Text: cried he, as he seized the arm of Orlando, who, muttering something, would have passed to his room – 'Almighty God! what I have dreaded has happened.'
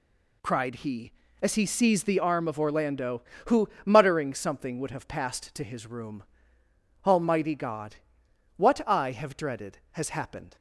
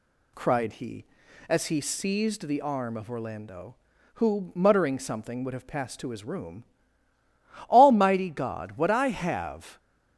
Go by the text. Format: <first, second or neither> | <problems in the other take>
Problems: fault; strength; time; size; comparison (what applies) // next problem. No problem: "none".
first | stops before "dreaded has happened"; at 9.7 s